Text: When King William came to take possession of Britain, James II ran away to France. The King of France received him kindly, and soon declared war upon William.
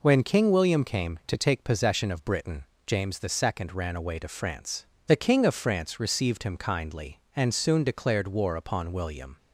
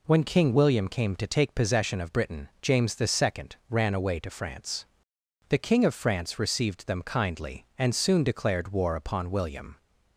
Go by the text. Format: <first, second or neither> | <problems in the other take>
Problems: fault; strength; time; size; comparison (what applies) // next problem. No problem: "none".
first | says "them" for "him"; at 6.8 s